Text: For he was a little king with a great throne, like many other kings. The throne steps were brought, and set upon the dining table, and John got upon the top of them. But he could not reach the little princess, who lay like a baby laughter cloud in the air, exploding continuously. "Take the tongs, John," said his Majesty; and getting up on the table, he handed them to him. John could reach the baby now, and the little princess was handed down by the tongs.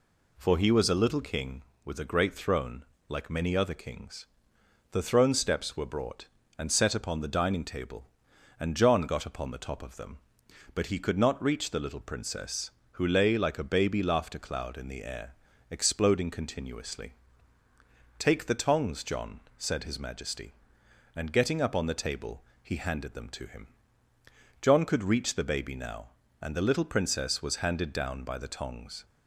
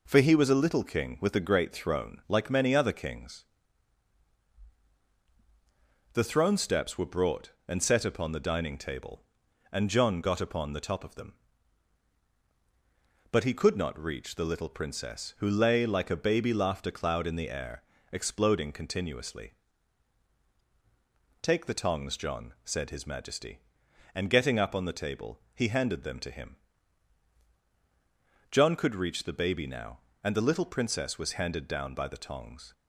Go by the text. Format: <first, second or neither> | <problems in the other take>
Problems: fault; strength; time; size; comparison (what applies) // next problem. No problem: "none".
neither | none